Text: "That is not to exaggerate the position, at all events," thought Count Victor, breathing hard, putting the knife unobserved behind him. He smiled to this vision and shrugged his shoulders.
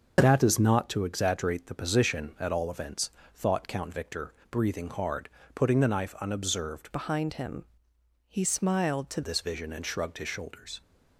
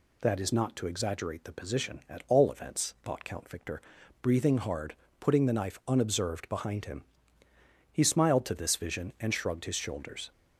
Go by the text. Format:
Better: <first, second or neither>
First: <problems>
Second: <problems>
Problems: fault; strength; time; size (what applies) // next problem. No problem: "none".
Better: second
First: starts louder than the rest; noticeable; until 1.1 s; 6 dB // changes voice from "behind" to "to"; from 6.9 to 9.2 s; 2.3 s long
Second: none